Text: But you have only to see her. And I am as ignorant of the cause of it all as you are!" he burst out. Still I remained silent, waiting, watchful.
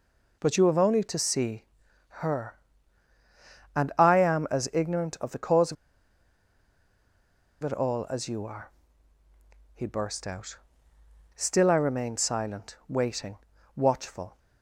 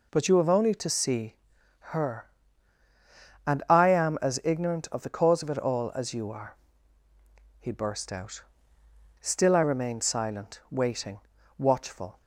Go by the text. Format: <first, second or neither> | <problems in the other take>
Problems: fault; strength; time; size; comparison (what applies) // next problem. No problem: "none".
second | pauses between "see" and "her"; at 1.6 s; 0.44 s long; also in the second // pauses between "of" and "it"; strong; at 5.7 s; 1.8 s long